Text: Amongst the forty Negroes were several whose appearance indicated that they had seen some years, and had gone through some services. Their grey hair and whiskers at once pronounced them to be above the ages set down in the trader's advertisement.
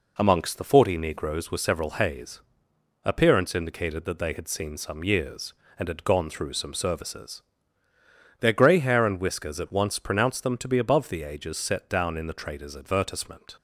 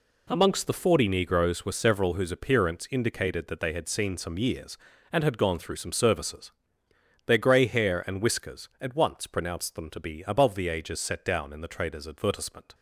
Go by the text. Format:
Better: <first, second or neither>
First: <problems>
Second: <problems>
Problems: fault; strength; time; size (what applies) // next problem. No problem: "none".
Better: second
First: says "hays" for "whose"; at 1.8 s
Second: none